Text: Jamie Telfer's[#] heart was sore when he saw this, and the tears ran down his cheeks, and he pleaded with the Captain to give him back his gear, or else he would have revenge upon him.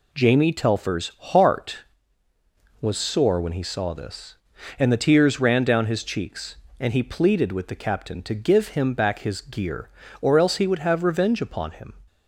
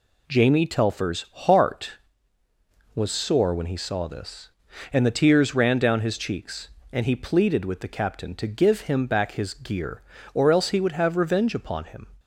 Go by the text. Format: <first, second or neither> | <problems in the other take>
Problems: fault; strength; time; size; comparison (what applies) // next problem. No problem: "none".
neither | none